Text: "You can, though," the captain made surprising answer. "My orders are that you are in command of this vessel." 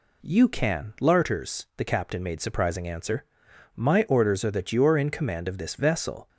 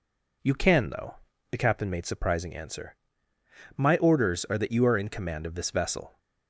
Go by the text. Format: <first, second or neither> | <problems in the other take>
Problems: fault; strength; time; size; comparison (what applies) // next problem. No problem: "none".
second | says "larters" for "though"; at 1.0 s